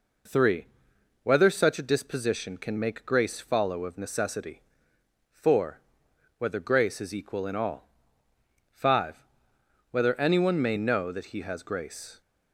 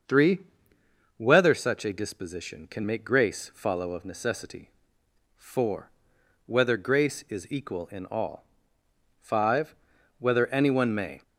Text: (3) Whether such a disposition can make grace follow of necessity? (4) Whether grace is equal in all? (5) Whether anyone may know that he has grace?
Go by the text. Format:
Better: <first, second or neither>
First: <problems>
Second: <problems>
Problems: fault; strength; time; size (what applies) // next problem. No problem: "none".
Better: first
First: none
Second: starts louder than the rest; until 1.8 s; 6.5 dB // stops before "know that he has grace"; at 11.2 s